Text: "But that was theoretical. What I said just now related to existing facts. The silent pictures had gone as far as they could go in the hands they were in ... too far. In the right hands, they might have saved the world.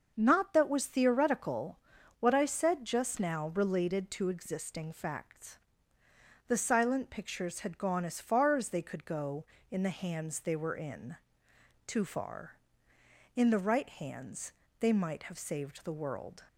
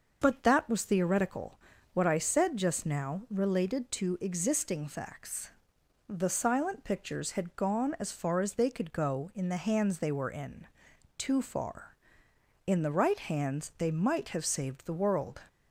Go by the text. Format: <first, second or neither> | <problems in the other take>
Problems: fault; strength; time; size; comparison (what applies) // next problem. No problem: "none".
second | starts louder than the rest; noticeable; until 1.1 s; 6 dB; also in the second // says "Not" for "But"; at 0.1 s